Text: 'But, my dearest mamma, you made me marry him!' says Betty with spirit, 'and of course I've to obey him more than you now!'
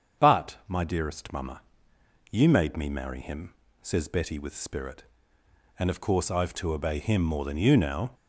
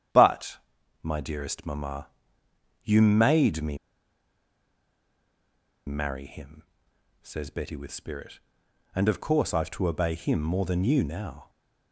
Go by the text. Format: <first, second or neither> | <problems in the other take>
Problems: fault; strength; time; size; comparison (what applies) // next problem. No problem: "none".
first | starts louder than the rest; strong; until 1.5 s; 9.5 dB; strong in the first // pauses between "me" and "marry"; strong; at 3.7 s; 2.1 s long